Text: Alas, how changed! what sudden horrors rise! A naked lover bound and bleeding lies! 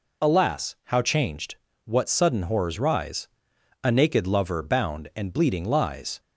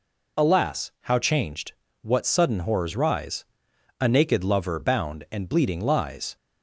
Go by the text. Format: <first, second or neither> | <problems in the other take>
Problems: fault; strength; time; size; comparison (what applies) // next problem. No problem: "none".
neither | none